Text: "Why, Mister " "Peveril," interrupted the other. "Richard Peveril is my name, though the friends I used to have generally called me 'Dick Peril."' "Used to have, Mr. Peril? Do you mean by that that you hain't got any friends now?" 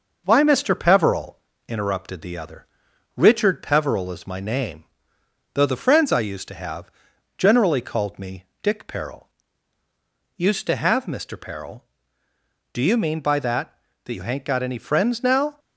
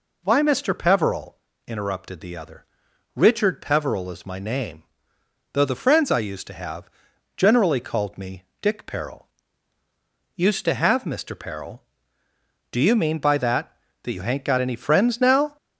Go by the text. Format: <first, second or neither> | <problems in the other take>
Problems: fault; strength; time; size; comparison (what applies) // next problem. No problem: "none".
second | gets quieter; slight; throughout; 2.5 dB // pauses between "have" and "generally"; noticeable; at 6.8 s; 0.46 s long; noticeable in the second // pauses between "me" and "Dick"; slight; at 8.4 s; 0.16 s long; slight in the second